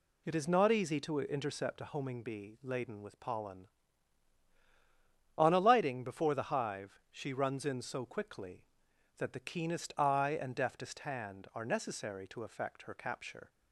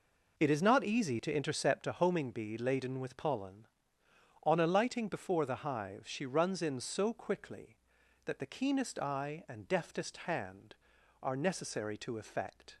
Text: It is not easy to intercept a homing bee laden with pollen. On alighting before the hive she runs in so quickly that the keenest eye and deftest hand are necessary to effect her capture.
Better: first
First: none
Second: stops before "her capture"; at 12.7 s

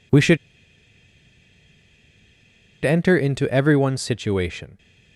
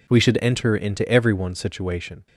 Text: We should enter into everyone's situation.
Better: second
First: pauses between "should" and "enter"; strong; at 0.3 s; 2.4 s long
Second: none

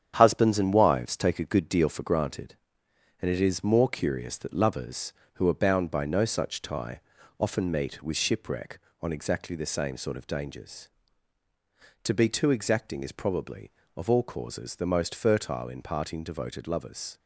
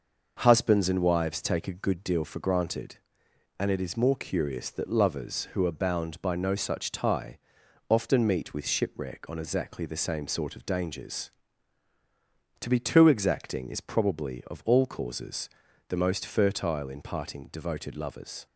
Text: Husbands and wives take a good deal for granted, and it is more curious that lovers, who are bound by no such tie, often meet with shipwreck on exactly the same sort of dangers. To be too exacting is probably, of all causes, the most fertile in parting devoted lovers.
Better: second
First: gets quieter; noticeable; throughout; 6 dB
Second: none

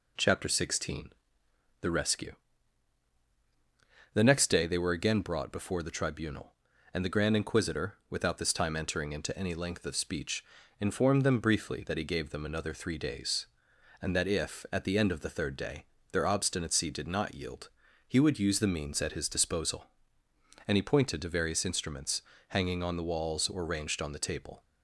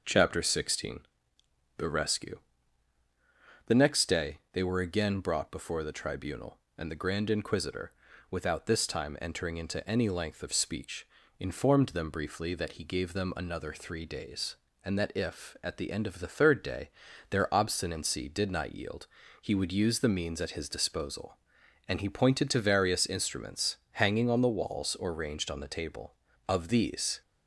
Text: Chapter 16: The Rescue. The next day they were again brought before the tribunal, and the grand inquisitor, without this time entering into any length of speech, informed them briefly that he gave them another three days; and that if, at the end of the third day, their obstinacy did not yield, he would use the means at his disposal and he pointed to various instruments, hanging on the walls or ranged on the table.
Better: first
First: none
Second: starts louder than the rest; noticeable; until 1.8 s; 6 dB // goes on to say "Of these"; noticeable; from 26.4 s on; 0.74 s long

